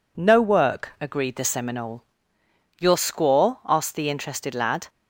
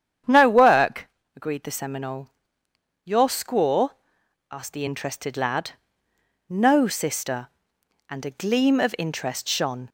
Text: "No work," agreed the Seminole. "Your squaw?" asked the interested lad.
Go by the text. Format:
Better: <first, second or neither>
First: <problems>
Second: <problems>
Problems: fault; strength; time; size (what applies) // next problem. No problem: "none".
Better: first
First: none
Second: starts louder than the rest; strong; until 1.5 s; 9 dB // goes on to say "No sister and a gleam of interest shone"; strong; from 6.4 s on; 3.4 s long